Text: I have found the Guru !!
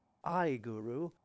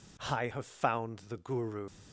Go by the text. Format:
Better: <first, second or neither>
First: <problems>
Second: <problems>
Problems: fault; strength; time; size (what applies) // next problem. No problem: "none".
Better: second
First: skips "have found the"; at 0.5 s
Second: none